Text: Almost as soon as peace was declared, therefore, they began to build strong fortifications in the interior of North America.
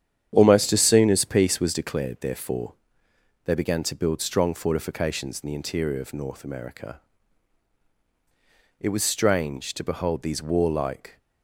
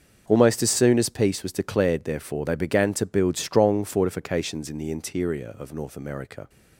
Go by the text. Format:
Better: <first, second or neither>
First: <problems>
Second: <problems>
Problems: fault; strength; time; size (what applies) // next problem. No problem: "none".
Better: second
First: starts louder than the rest; strong; until 1.3 s; 9 dB // goes on to say "It was strange to behold these warlike"; strong; from 8.8 s on; 2.3 s long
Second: starts louder than the rest; until 1.3 s; 6.5 dB